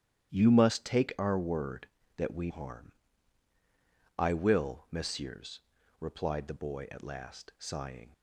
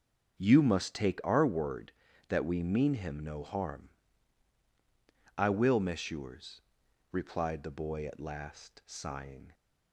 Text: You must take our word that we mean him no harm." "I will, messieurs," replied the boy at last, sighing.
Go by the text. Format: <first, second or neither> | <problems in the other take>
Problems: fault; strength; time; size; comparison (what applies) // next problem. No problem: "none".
second | starts louder than the rest; strong; until 1.3 s; 10.5 dB; also in the second // skips "mean him no"; at 2.5 s